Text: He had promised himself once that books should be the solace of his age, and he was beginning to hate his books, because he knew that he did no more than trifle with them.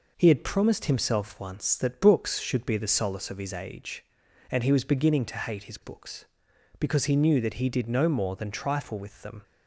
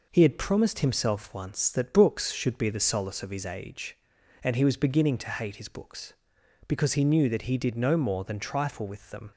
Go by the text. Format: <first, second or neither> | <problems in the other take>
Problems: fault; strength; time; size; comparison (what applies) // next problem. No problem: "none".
neither | none